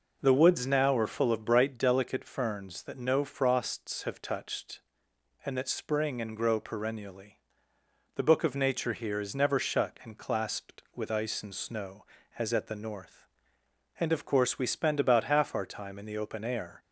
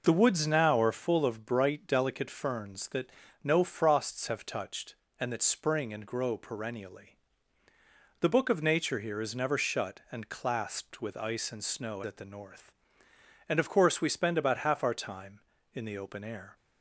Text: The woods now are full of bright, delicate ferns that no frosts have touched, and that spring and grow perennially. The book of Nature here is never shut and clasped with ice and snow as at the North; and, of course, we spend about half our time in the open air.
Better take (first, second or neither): first